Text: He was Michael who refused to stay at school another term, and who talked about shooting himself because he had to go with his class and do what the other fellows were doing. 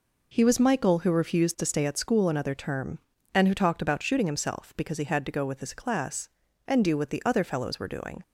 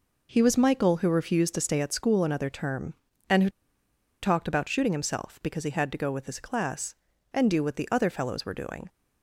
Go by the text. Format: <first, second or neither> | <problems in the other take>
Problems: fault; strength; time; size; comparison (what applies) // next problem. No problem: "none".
first | pauses between "who" and "talked"; noticeable; at 3.5 s; 0.72 s long